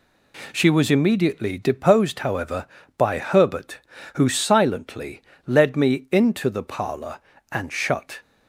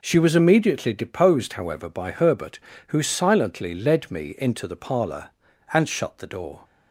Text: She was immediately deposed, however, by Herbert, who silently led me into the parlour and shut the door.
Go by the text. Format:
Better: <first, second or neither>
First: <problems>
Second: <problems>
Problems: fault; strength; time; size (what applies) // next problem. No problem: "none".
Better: second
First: pauses between "silently" and "led"; slight; at 5.2 s; 0.26 s long // stops before "the door"; at 8.2 s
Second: none